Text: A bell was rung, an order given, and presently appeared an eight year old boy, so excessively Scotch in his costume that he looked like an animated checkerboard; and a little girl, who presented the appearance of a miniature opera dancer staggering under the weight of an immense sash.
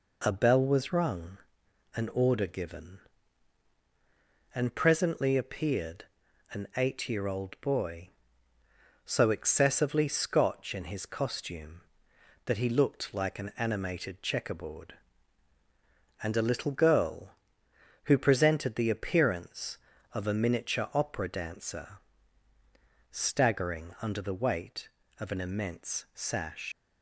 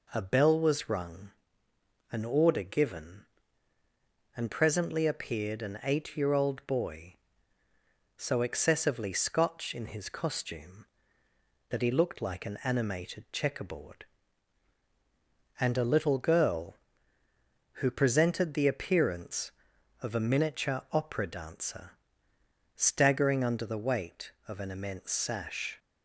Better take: second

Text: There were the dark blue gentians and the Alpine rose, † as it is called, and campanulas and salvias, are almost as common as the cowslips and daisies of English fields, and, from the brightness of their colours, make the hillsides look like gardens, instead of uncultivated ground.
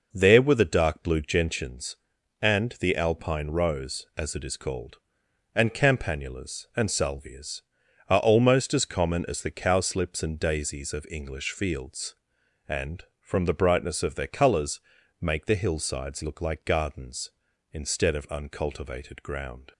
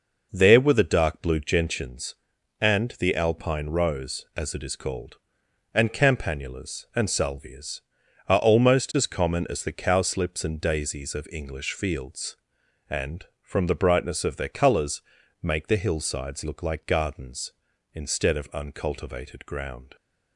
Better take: neither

